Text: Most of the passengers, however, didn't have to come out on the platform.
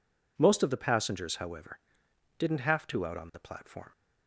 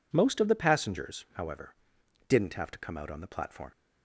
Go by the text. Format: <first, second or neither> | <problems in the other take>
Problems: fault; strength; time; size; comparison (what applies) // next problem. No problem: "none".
second | skips "come"; at 3.0 s